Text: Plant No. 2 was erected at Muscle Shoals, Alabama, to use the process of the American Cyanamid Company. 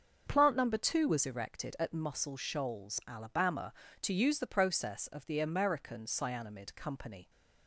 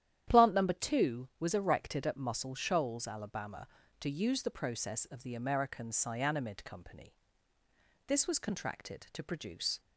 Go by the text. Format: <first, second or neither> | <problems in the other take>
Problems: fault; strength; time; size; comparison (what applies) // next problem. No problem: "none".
first | starts louder than the rest; strong; until 1.4 s; 10.5 dB; also in the first // goes on to say "This was contracted to produce"; strong; from 8.0 s on; 1.7 s long